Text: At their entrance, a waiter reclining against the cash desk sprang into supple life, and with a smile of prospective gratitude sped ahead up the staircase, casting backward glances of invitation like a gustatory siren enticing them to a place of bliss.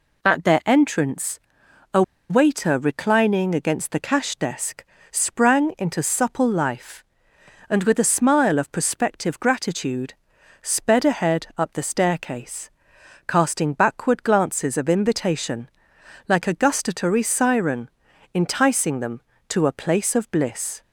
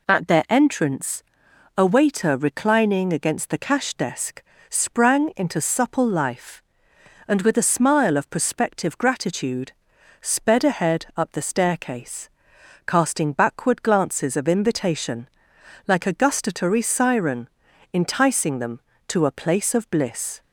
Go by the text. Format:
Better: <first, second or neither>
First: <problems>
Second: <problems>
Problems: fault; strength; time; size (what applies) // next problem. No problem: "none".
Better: second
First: pauses between "a" and "waiter"; slight; at 2.0 s; 0.27 s long // pauses between "desk" and "sprang"; slight; at 4.8 s; 0.26 s long // pauses between "gratitude" and "sped"; noticeable; at 10.1 s; 0.48 s long // pauses between "invitation" and "like"; noticeable; at 15.6 s; 0.60 s long // pauses between "siren" and "enticing"; at 17.8 s; 0.42 s long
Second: pauses between "desk" and "sprang"; slight; at 4.4 s; 0.26 s long // pauses between "gratitude" and "sped"; noticeable; at 9.7 s; 0.48 s long // pauses between "invitation" and "like"; noticeable; at 15.2 s; 0.60 s long // pauses between "siren" and "enticing"; at 17.4 s; 0.42 s long